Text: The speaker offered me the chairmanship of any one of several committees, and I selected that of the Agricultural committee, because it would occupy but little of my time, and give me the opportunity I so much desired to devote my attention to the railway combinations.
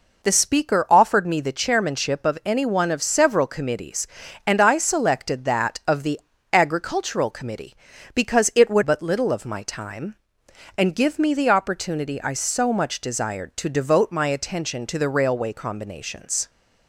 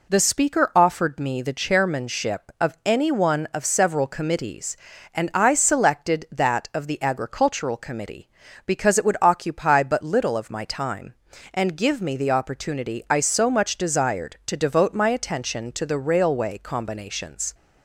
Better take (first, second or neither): second